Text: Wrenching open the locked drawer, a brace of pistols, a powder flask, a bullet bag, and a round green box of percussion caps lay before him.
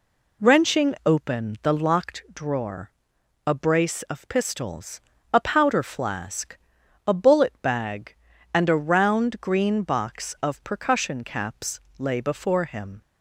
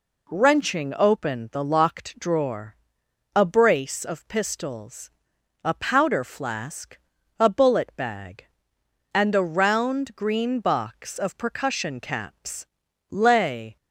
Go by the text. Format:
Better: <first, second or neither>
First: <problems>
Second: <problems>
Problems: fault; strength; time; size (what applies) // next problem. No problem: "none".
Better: first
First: pauses between "caps" and "lay"; slight; at 11.8 s; 0.18 s long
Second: pauses between "caps" and "lay"; at 12.6 s; 0.42 s long // stops before "before him"; at 13.7 s